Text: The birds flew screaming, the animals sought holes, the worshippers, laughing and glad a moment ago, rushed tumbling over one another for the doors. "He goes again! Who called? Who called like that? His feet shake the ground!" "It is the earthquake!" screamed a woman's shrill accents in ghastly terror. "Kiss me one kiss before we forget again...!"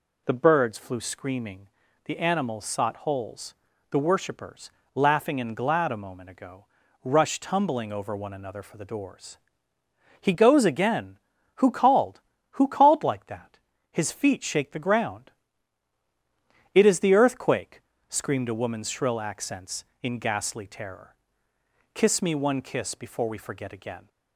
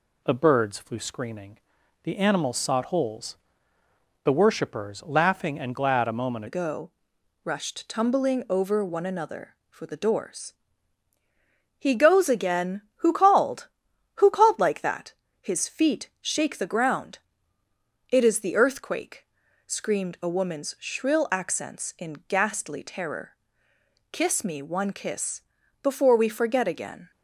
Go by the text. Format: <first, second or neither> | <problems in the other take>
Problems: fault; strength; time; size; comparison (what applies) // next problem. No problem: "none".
first | changes voice at "ago"; from 6.4 s on; 20.7 s long // pauses between "kiss" and "before"; at 25.4 s; 0.42 s long